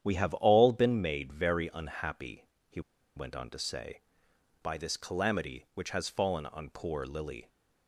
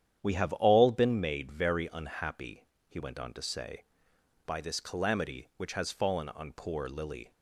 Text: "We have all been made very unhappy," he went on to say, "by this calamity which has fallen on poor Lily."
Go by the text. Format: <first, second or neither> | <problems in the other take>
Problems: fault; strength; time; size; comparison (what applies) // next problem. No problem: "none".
second | starts louder than the rest; strong; until 1.0 s; 9.5 dB; strong in the second // pauses between "he" and "went"; slight; at 2.8 s; 0.35 s long